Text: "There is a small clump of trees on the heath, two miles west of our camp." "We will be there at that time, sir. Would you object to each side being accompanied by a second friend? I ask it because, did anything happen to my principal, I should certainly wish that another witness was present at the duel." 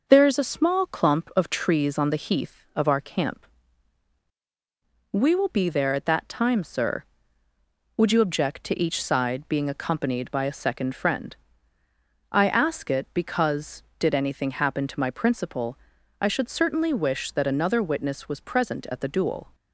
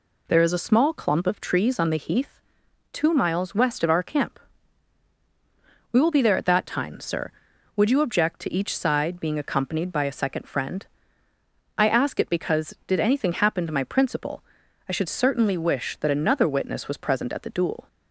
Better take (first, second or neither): second